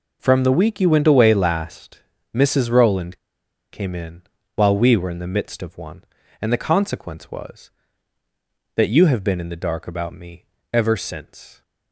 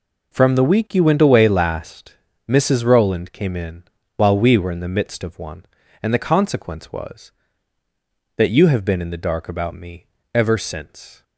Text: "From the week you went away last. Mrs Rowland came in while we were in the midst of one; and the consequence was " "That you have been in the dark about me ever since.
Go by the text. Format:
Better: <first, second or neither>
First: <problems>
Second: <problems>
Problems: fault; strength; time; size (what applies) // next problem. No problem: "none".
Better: second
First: pauses between "Rowland" and "came"; noticeable; at 3.1 s; 0.55 s long // pauses between "in" and "while"; slight; at 4.2 s; 0.32 s long // pauses between "me" and "ever"; slight; at 10.4 s; 0.26 s long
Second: pauses between "in" and "while"; slight; at 3.8 s; 0.32 s long // pauses between "me" and "ever"; slight; at 10.0 s; 0.26 s long